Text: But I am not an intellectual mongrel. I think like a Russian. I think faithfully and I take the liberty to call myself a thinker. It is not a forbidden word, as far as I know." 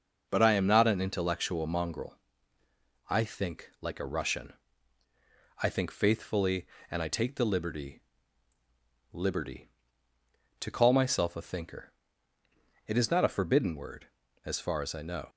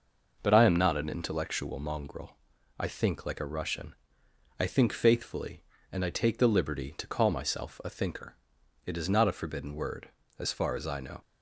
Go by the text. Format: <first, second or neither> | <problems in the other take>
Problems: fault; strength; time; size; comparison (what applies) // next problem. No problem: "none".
second | says "liberty" twice; at 9.1 s